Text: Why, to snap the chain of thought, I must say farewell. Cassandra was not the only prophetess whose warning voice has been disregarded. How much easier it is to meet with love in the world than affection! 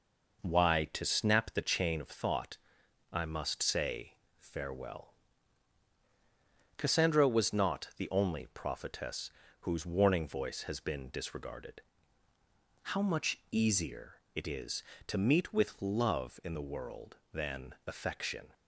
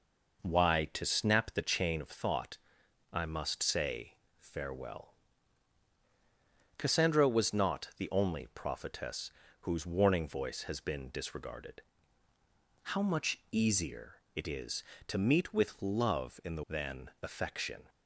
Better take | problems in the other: first | pauses between "say" and "farewell"; slight; at 4.1 s; 0.24 s long; slight in the first // pauses between "prophetess" and "whose"; slight; at 9.3 s; 0.30 s long; slight in the first // skips "world"; at 16.6 s

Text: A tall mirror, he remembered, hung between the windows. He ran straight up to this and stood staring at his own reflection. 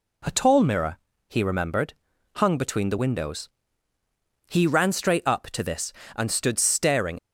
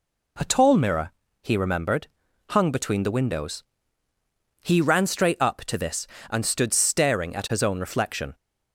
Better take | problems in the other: second | stops before "at his own reflection"; at 7.1 s

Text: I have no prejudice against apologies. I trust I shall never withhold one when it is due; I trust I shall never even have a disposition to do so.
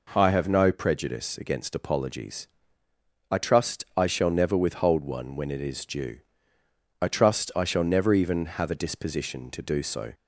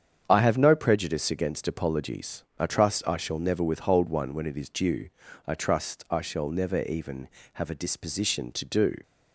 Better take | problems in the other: first | starts louder than the rest; strong; until 1.2 s; 8 dB // stops before "so"; at 9.0 s

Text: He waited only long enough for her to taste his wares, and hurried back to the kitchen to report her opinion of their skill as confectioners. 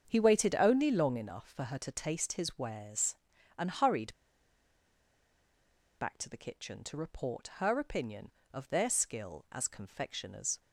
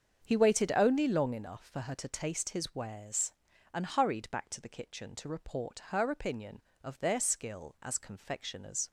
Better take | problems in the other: second | starts louder than the rest; strong; until 1.0 s; 7 dB; strong in the second // pauses between "hurried" and "back"; strong; at 4.1 s; 1.8 s long

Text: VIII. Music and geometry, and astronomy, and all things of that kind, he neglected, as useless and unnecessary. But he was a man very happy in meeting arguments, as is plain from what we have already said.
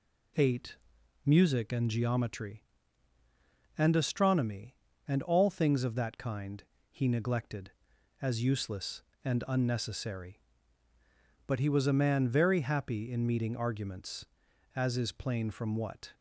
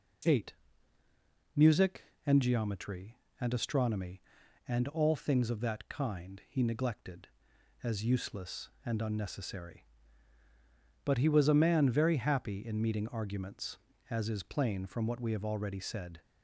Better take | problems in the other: second | stops before "we have already said"; at 16.1 s

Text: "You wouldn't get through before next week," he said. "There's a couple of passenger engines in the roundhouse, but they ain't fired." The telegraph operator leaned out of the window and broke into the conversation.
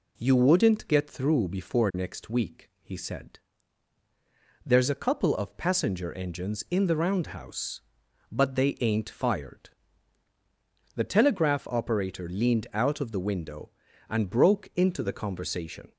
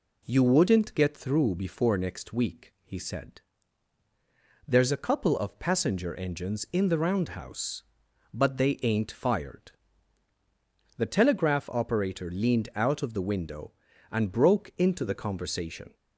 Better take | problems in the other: neither | none

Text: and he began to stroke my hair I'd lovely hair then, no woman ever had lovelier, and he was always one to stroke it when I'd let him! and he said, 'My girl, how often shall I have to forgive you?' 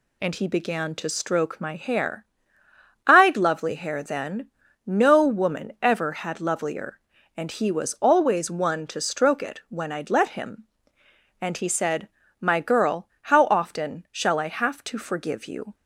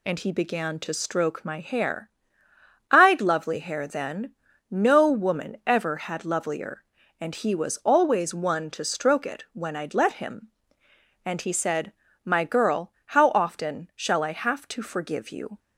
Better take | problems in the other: neither | pauses between "hair" and "I'd"; noticeable; the same in both

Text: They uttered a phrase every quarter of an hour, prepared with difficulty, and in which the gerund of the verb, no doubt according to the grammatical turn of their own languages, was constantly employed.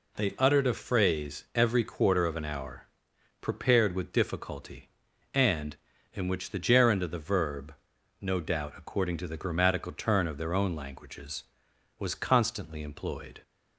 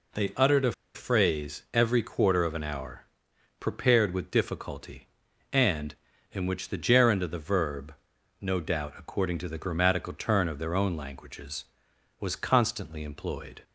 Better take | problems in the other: first | pauses between "a" and "phrase"; slight; at 0.7 s; 0.22 s long

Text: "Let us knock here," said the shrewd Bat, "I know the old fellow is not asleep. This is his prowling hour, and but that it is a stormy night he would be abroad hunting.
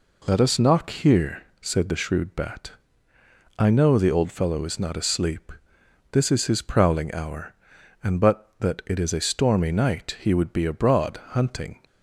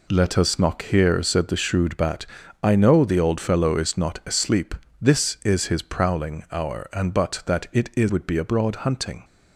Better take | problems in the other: first | skips "a stormy night he"; at 8.0 s

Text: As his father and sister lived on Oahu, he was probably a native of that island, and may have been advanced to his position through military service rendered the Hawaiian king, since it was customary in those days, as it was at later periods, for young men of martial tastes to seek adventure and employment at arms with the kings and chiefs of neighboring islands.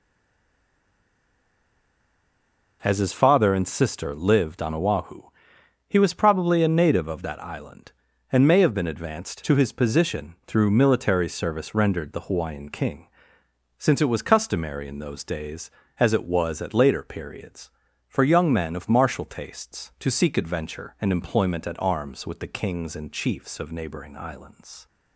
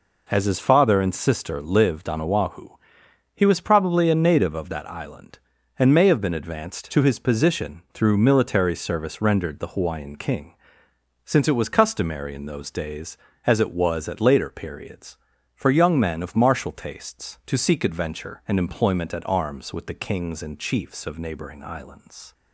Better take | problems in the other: second | stays silent before the first word; strong; until 2.8 s; 2.8 s long

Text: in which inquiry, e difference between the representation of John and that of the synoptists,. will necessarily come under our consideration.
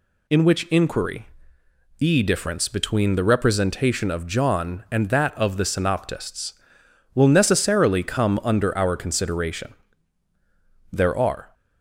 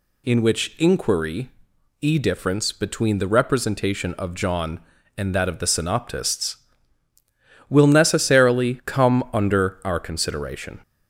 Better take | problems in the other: second | goes on to say "There are"; noticeable; from 10.9 s on; 0.62 s long

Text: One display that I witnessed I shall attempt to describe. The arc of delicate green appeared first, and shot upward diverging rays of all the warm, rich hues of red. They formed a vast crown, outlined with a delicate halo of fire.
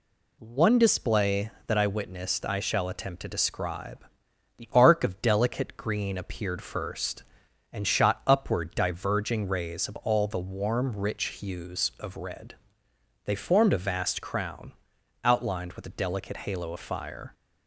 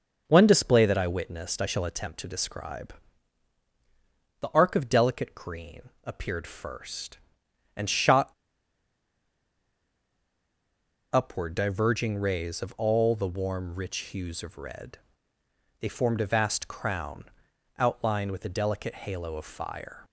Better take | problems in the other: first | pauses between "green" and "appeared"; slight; at 5.8 s; 0.16 s long // pauses between "shot" and "upward"; strong; at 8.3 s; 2.7 s long

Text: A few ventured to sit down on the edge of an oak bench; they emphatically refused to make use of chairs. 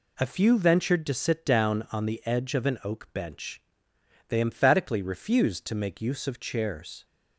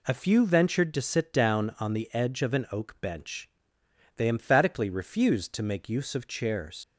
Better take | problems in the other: first | leaves "chairs" unfinished; at 6.8 s; 90 ms

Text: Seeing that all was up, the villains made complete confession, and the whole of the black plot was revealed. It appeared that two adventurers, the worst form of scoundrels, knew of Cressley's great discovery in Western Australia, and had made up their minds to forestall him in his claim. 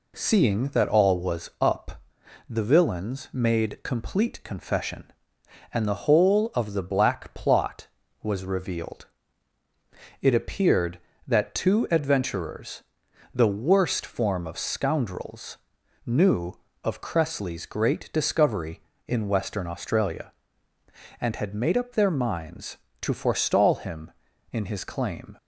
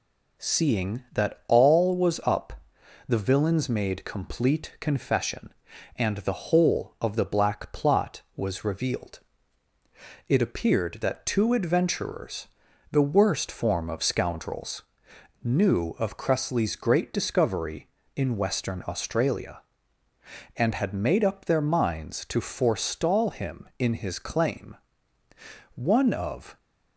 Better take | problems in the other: first | goes on to say "One of"; noticeable; from 25.7 s on; 0.82 s long

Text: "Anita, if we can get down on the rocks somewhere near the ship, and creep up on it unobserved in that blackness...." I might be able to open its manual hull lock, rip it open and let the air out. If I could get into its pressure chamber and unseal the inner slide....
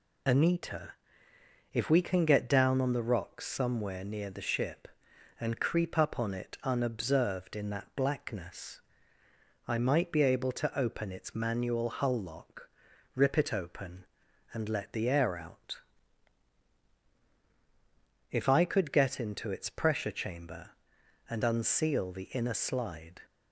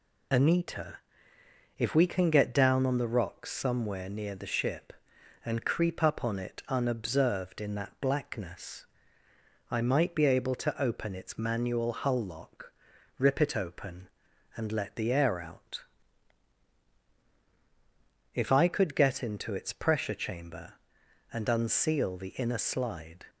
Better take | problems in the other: neither | none

